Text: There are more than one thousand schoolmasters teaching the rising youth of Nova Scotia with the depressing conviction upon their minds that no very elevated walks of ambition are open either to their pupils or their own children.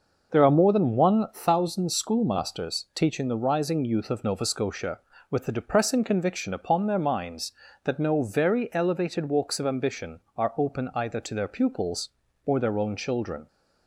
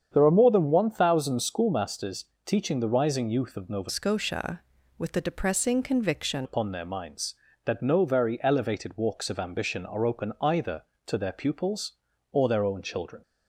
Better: first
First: none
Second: starts louder than the rest; strong; until 1.1 s; 8 dB // pauses between "schoolmasters" and "teaching"; slight; at 2.2 s; 0.18 s long // changes voice from "Scotia" to "conviction"; from 3.8 to 6.4 s; 2.6 s long

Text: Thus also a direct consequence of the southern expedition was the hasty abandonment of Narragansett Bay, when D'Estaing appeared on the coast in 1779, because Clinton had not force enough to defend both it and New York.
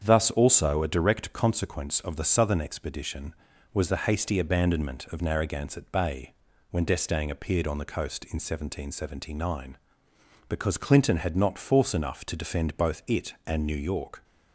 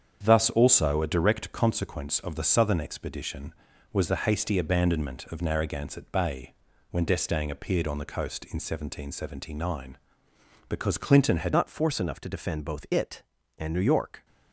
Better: first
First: starts louder than the rest; strong; until 1.0 s; 7.5 dB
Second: starts louder than the rest; strong; until 1.2 s; 7.5 dB // changes voice at "not"; from 11.5 s on; 2.7 s long

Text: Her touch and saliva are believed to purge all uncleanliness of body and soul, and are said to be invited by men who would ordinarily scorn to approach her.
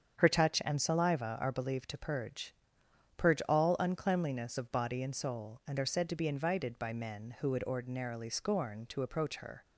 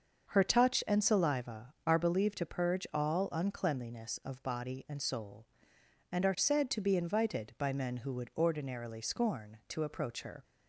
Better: second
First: starts louder than the rest; strong; until 1.2 s; 8 dB // says "purge" twice; at 3.1 s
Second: starts louder than the rest; until 1.3 s; 6.5 dB

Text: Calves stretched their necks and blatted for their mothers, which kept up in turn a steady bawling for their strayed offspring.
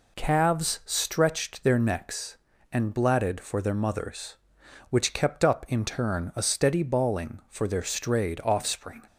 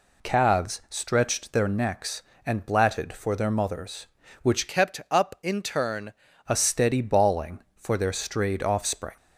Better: first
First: none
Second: changes voice from "kept" to "turn"; from 4.6 to 6.1 s; 1.5 s long

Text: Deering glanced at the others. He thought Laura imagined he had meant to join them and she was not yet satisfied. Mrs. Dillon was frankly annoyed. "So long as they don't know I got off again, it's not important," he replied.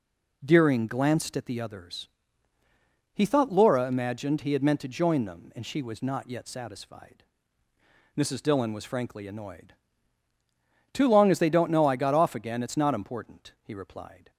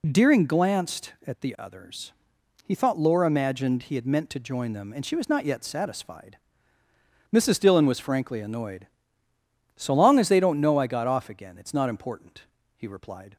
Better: second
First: says "Too" for "So"; at 10.9 s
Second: none

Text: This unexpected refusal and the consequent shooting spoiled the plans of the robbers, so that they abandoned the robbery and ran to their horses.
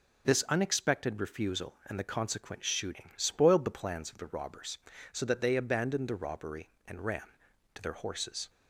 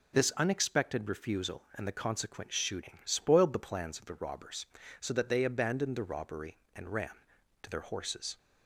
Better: neither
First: none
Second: none

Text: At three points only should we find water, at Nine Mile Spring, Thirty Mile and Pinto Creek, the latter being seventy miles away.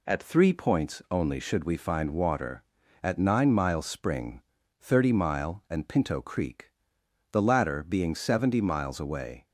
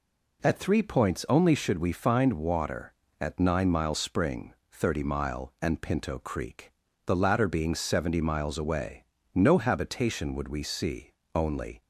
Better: first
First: none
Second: goes on to say "No habitation would we see only"; strong; from 9.3 s on; 2.4 s long

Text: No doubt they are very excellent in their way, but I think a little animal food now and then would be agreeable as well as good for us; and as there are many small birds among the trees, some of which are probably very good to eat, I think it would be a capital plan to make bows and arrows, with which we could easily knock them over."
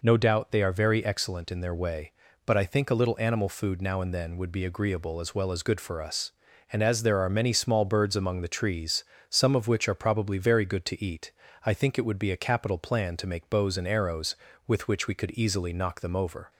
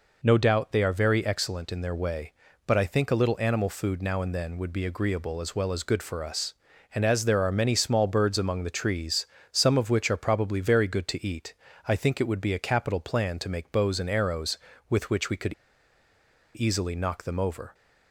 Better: first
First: none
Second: pauses between "could" and "easily"; at 15.5 s; 1.0 s long

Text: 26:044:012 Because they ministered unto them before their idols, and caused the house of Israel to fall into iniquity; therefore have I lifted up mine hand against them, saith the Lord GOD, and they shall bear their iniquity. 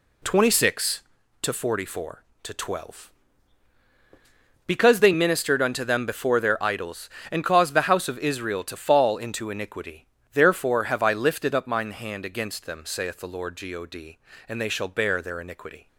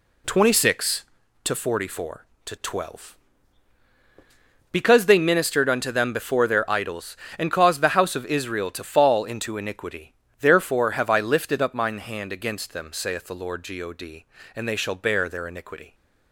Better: neither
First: none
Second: none

